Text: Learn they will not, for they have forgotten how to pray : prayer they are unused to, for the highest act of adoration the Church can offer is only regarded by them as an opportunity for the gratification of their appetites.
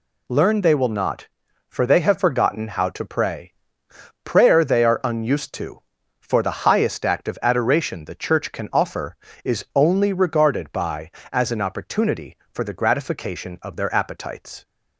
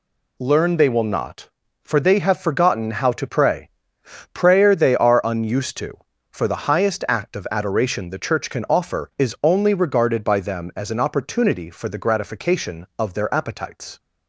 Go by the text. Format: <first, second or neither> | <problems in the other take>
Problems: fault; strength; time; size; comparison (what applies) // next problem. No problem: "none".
second | skips "them"; at 11.2 s